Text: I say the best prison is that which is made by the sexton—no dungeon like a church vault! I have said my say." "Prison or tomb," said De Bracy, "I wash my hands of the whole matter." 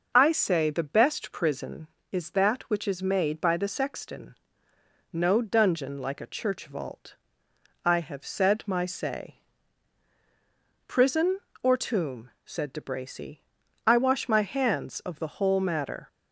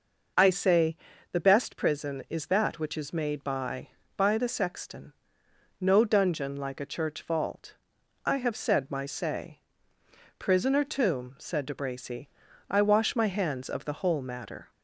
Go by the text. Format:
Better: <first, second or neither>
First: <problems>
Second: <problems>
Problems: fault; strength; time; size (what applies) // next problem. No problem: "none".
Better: first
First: none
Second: pauses between "say" and "the"; slight; at 0.9 s; 0.34 s long // says "by" twice; at 4.1 s